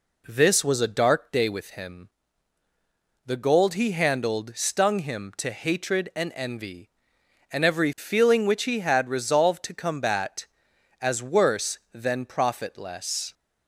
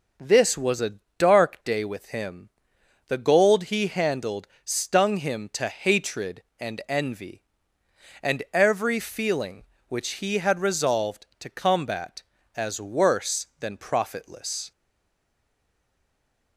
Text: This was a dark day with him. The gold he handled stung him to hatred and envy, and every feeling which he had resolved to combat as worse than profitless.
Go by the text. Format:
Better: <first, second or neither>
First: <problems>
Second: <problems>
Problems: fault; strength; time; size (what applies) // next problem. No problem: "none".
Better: first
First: none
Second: starts louder than the rest; noticeable; until 1.4 s; 6 dB // pauses between "a" and "dark"; slight; at 0.9 s; 0.22 s long // pauses between "handled" and "stung"; slight; at 4.4 s; 0.18 s long // stays silent after the last word; noticeable; from 14.7 s on; 1.8 s long